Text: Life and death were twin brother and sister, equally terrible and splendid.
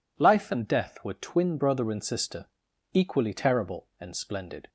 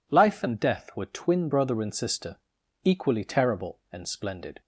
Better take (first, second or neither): neither